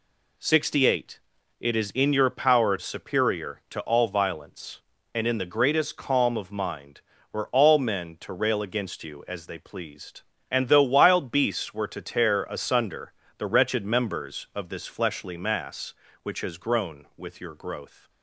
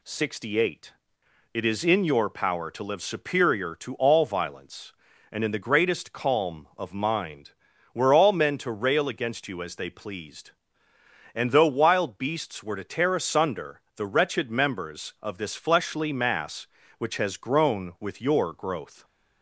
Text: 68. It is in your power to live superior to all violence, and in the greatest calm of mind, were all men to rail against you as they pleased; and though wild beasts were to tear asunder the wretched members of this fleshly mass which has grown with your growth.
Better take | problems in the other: second | skips "to live"; at 2.7 s // pauses between "asunder" and "the"; slight; at 13.1 s; 0.24 s long

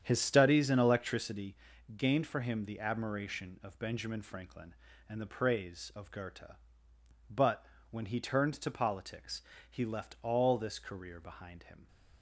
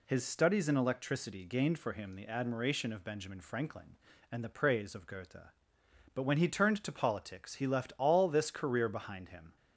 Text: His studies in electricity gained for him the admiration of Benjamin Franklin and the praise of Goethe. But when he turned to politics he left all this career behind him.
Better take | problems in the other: second | starts louder than the rest; strong; until 1.2 s; 8.5 dB // pauses between "electricity" and "gained"; at 1.5 s; 0.40 s long // pauses between "But" and "when"; slight; at 7.6 s; 0.24 s long // pauses between "politics" and "he"; slight; at 9.4 s; 0.28 s long

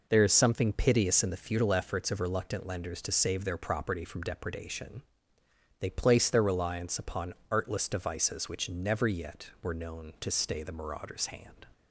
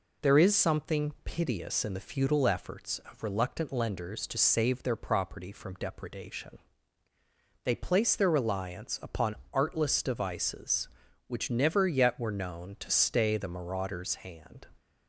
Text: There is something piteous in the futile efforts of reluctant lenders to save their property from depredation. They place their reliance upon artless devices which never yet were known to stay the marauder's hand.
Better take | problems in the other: neither | pauses between "upon" and "artless"; slight; the same in both

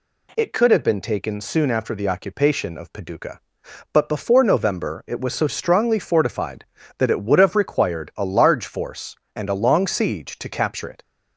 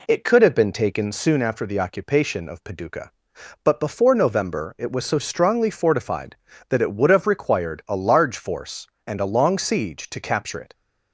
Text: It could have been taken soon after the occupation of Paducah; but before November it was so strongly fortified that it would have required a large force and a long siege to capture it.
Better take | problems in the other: first | starts louder than the rest; slight; until 1.4 s; 2.5 dB

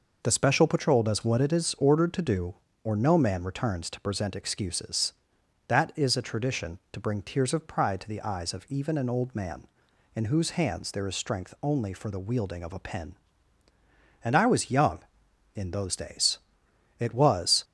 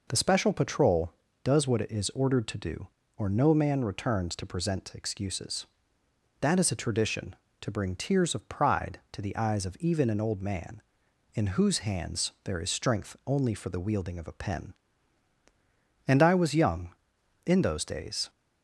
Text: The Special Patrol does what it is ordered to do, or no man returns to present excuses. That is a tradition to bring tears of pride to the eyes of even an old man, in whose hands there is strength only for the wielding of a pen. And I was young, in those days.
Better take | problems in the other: second | goes on to say "It was"; noticeable; from 16.9 s on; 0.64 s long

